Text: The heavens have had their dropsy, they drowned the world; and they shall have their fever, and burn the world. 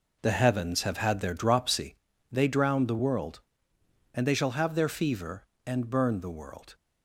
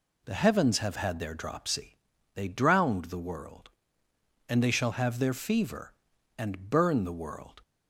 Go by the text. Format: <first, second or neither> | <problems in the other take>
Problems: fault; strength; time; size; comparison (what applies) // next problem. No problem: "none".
second | starts louder than the rest; noticeable; until 1.8 s; 4.5 dB